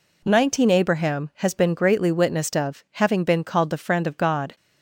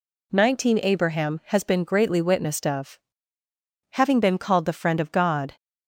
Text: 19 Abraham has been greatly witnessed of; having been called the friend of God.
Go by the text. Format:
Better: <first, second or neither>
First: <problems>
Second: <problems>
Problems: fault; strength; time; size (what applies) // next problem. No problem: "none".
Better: neither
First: none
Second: none